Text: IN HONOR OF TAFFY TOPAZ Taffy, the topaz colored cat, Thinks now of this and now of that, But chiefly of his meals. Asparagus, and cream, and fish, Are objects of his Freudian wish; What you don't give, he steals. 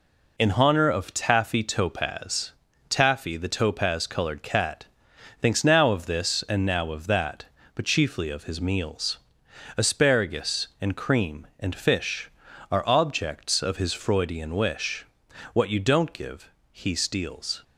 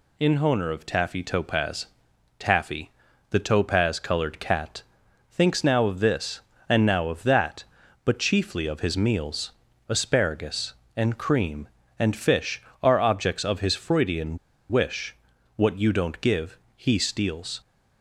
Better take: first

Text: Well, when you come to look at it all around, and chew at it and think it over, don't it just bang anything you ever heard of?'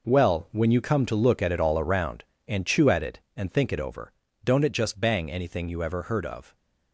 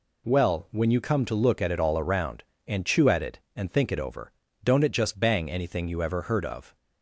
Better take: second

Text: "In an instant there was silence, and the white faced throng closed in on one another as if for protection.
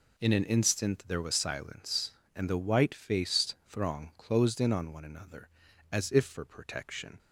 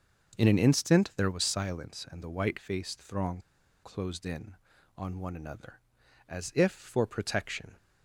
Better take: first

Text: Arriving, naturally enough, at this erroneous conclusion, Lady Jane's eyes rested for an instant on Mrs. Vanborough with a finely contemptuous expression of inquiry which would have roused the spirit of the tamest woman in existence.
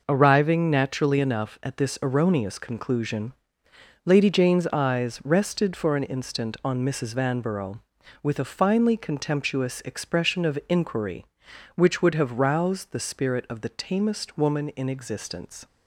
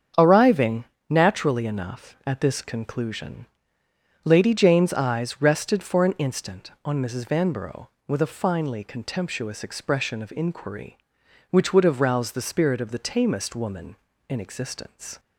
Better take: first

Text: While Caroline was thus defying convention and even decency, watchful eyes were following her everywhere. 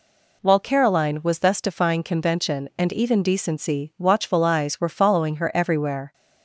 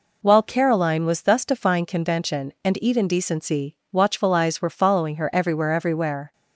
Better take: first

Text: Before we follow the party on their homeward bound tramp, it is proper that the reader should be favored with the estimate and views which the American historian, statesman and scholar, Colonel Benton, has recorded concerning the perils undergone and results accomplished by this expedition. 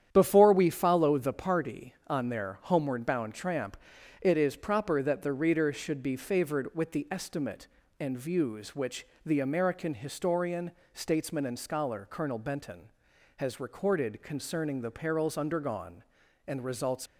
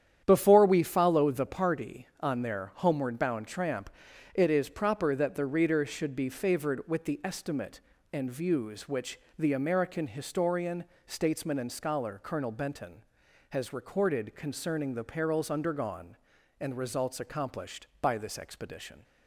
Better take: second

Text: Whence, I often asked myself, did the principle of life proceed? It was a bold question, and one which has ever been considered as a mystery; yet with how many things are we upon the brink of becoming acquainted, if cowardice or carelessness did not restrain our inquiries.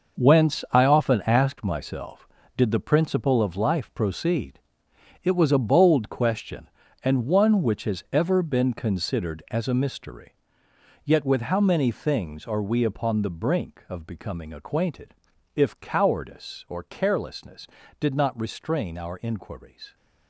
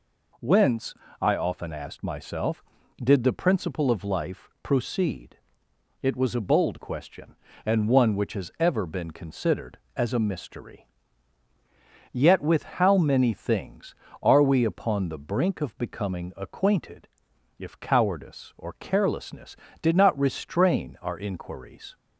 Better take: second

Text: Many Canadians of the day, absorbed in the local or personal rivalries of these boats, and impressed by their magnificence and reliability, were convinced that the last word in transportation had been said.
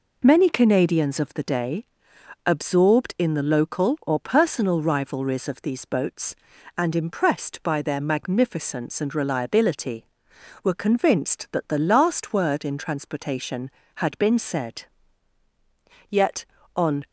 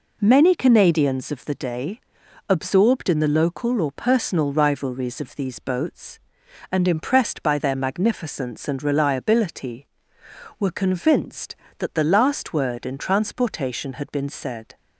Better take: second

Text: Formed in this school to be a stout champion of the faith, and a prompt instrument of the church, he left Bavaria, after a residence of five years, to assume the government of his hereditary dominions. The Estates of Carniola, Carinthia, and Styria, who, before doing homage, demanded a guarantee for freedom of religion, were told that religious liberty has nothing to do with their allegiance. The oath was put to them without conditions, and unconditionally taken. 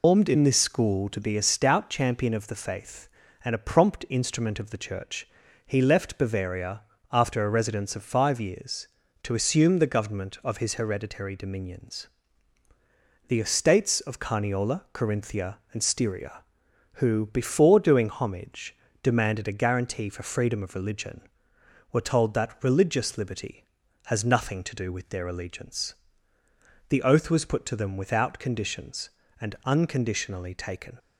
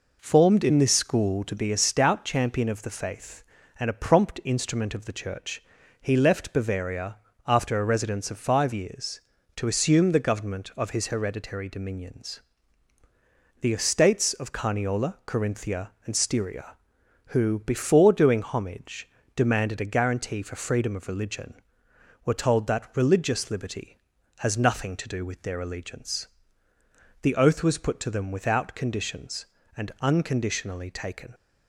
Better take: second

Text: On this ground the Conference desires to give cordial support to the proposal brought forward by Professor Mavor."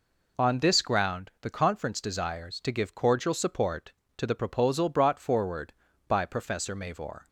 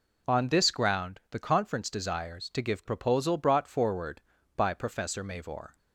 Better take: first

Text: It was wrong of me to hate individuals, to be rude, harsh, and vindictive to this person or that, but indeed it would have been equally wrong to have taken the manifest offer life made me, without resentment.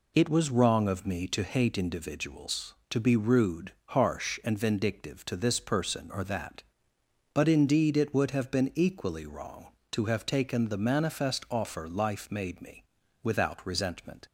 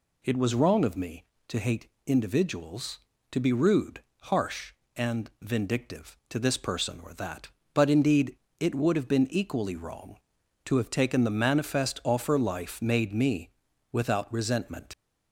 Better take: first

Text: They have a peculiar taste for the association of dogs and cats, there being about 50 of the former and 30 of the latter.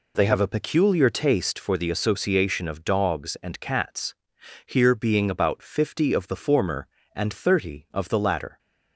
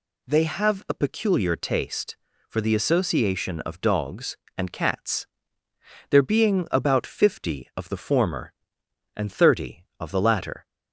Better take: second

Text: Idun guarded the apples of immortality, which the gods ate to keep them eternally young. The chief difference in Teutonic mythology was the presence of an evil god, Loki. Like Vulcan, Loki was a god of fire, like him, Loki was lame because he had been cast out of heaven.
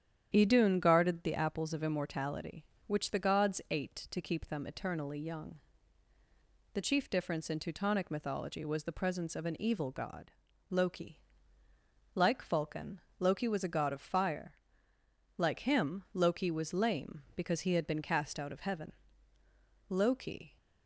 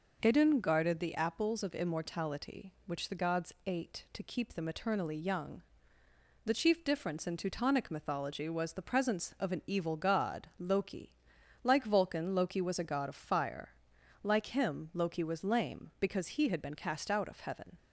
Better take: second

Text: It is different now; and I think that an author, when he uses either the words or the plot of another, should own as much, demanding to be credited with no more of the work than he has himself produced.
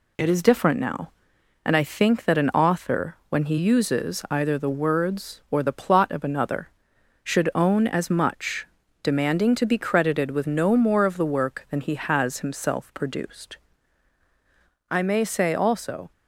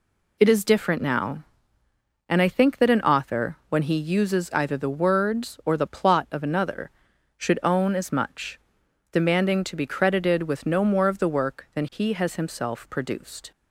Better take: second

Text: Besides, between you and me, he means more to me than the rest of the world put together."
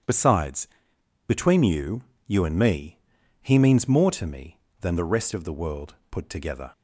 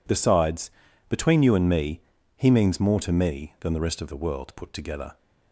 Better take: second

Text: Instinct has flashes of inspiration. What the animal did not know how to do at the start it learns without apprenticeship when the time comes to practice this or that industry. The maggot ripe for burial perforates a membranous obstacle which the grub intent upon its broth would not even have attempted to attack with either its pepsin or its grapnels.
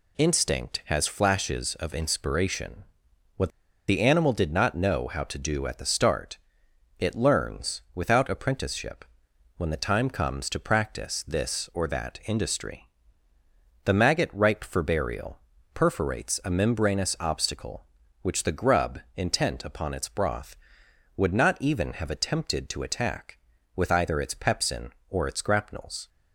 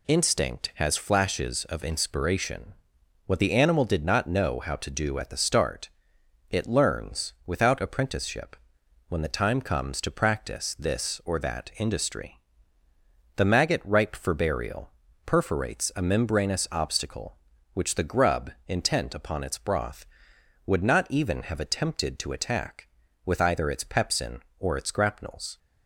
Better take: second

